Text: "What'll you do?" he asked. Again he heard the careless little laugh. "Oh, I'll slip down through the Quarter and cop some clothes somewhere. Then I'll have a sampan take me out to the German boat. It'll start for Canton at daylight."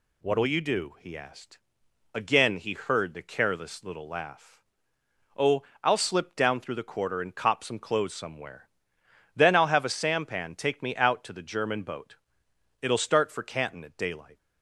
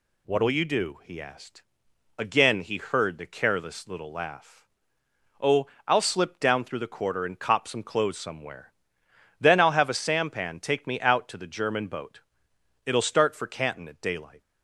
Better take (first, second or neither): neither